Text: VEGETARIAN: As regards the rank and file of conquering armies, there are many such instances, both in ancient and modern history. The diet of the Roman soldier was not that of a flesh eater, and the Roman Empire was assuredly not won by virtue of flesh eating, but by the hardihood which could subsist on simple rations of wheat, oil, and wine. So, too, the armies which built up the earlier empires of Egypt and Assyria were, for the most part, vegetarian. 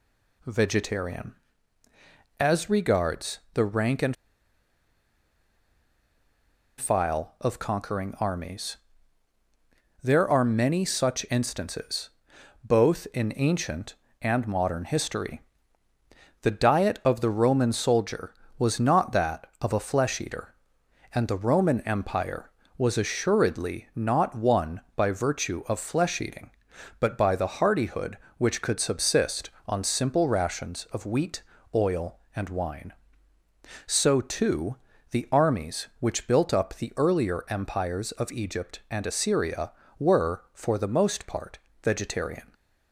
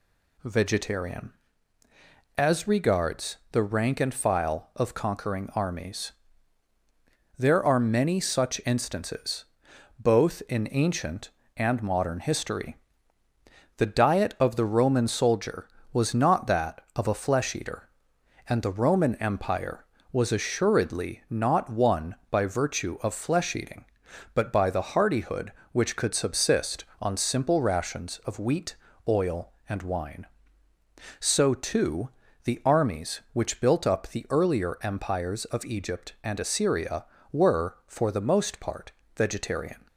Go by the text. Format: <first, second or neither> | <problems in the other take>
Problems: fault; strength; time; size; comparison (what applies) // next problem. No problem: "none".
second | pauses between "and" and "file"; strong; at 4.1 s; 2.6 s long